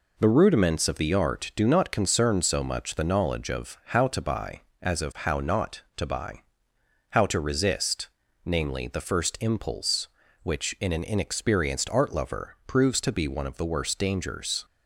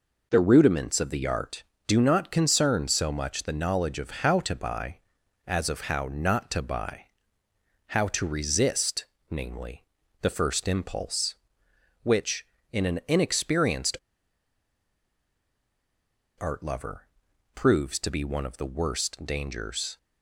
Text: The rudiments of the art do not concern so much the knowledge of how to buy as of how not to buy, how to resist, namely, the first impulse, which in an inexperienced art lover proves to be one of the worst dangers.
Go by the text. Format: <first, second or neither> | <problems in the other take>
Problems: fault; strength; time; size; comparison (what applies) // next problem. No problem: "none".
first | pauses between "inexperienced" and "art"; strong; at 13.9 s; 2.4 s long // pauses between "lover" and "proves"; noticeable; at 17.0 s; 0.48 s long